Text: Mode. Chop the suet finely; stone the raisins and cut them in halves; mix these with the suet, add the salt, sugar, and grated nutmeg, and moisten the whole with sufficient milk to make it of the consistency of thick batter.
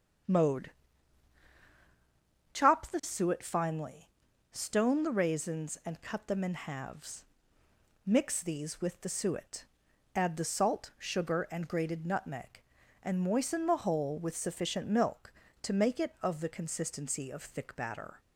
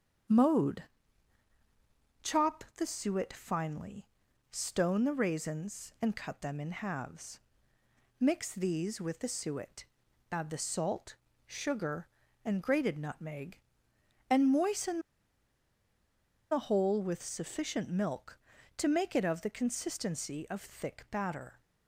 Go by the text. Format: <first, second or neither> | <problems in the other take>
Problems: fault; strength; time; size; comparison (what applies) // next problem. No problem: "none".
first | starts louder than the rest; strong; until 2.7 s; 7.5 dB; strong in the first // pauses between "moisten" and "the"; strong; at 14.9 s; 1.5 s long